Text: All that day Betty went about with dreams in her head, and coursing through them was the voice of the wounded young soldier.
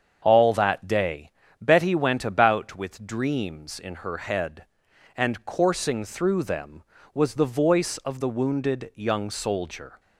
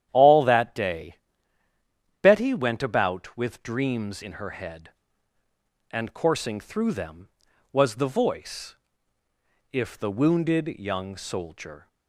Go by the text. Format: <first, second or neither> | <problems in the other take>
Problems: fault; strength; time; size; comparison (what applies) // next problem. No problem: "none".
first | starts louder than the rest; strong; until 1.1 s; 10.5 dB; strong in the first // pauses between "day" and "Betty"; at 1.1 s; 1.0 s long; slight in the first // says "if" for "of"; at 9.7 s